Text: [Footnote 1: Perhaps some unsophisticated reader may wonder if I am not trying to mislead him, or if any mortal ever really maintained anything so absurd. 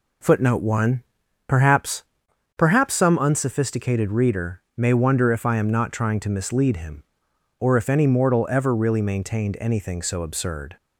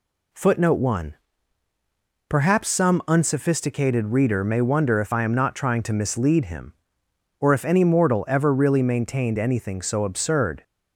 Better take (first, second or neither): second